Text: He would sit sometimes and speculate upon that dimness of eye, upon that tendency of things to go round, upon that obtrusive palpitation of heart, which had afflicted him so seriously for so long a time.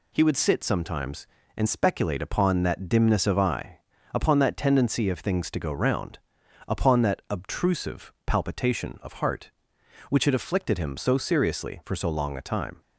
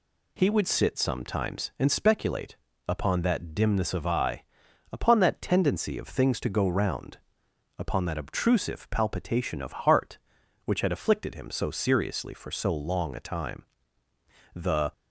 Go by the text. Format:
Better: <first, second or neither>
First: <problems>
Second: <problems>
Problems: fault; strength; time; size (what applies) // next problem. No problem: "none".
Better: first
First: none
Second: pauses between "speculate" and "upon"; slight; at 2.5 s; 0.30 s long // goes on to say "The"; slight; from 14.5 s on; 0.38 s long